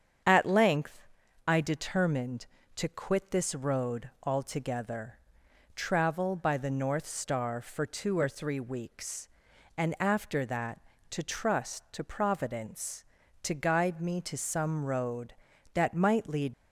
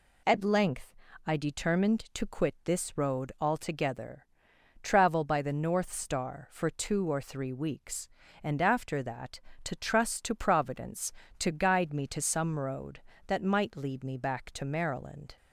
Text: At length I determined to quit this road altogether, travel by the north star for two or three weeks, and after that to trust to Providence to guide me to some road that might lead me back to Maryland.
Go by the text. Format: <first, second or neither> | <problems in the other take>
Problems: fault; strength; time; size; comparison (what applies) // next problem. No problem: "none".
second | starts louder than the rest; strong; until 1.6 s; 7.5 dB // pauses between "length" and "I"; at 1.0 s; 0.40 s long; slight in the second // stops before "me back to Maryland"; at 16.5 s